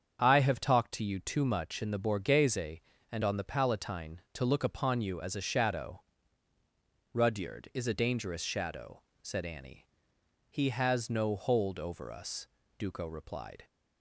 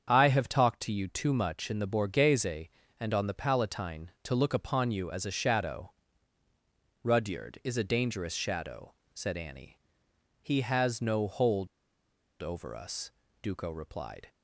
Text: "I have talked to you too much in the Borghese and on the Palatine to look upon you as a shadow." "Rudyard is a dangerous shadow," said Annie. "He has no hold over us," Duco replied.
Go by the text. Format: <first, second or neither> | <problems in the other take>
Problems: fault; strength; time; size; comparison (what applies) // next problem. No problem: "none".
first | starts louder than the rest; strong; until 1.1 s; 7.5 dB; strong in the first // pauses between "hold" and "over"; noticeable; at 11.6 s; 0.75 s long